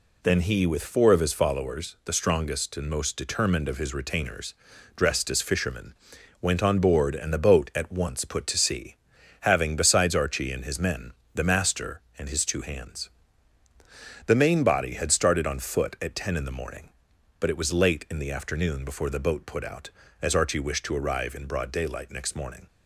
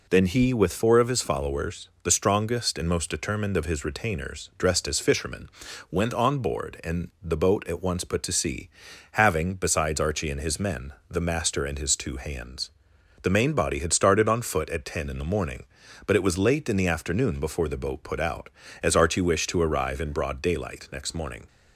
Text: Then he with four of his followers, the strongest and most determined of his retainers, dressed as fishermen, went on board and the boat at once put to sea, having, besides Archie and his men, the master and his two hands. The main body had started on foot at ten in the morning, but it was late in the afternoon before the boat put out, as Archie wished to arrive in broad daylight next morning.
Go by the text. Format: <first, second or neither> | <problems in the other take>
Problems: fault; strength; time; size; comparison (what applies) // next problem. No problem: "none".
neither | none